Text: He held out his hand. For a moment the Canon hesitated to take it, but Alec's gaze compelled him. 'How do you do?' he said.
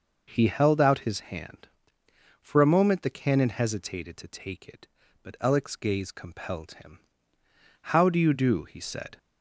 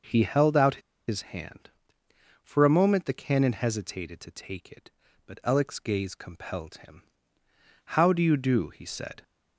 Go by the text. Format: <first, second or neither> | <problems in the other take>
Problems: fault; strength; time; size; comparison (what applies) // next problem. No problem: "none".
first | pauses between "out" and "his"; slight; at 0.8 s; 0.27 s long